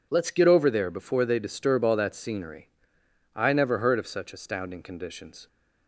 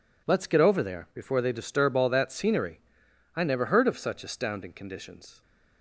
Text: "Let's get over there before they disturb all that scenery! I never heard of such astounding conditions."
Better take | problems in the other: neither | none

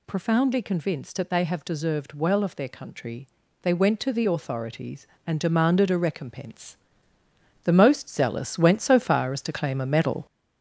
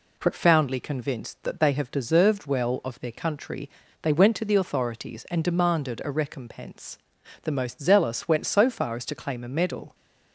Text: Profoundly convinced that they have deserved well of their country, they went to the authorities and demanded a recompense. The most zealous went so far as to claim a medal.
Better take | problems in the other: second | gets louder; noticeable; throughout; 5.5 dB

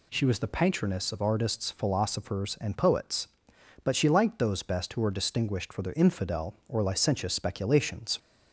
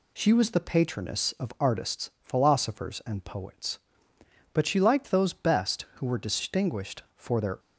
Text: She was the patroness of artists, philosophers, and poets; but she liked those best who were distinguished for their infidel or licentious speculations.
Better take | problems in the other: first | stops before "infidel or licentious speculations"; at 7.5 s

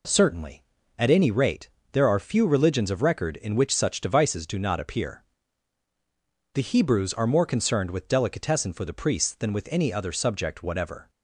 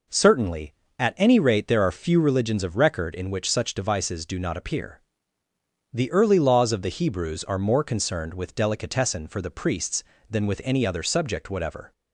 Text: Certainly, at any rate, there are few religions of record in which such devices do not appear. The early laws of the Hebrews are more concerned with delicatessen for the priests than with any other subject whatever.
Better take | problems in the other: second | skips "early laws of the"; at 6.6 s

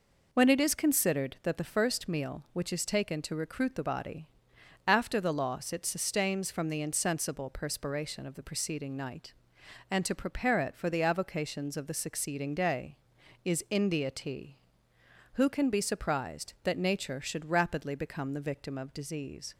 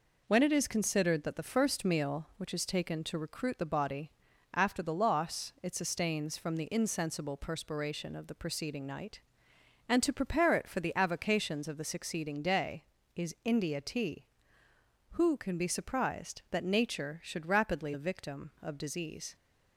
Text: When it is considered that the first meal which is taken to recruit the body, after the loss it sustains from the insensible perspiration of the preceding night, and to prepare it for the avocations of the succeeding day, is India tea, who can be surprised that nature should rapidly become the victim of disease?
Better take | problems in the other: first | skips "become"; at 17.9 s

